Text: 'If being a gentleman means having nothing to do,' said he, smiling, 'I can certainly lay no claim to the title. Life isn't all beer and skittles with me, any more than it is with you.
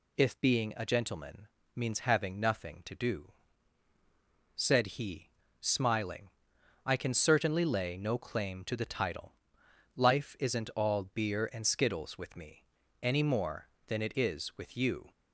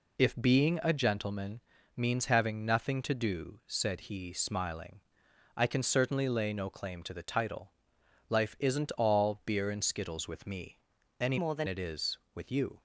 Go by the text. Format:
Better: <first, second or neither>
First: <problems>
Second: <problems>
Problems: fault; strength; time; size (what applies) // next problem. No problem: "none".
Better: first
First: pauses between "gentleman" and "means"; slight; at 1.4 s; 0.28 s long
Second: pauses between "gentleman" and "means"; slight; at 1.6 s; 0.36 s long // changes voice from "more" to "than"; from 11.3 to 11.6 s; 0.3 s long